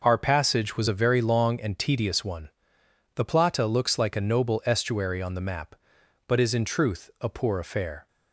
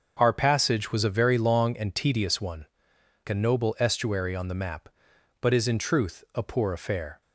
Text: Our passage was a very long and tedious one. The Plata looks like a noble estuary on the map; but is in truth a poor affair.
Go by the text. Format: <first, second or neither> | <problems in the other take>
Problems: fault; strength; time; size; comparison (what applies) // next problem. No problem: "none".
first | starts louder than the rest; until 1.1 s; 6.5 dB // skips "The Plata looks like"; at 2.9 s